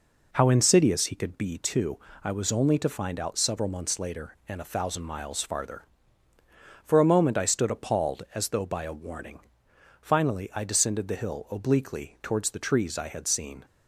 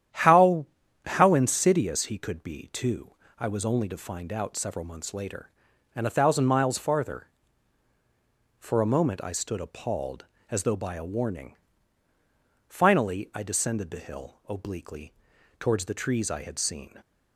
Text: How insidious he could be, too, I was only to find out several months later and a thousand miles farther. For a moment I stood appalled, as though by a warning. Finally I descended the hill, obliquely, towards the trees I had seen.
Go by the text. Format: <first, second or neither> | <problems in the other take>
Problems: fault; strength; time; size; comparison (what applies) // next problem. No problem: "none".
first | starts louder than the rest; strong; until 1.5 s; 10 dB // says "How" twice; at 1.0 s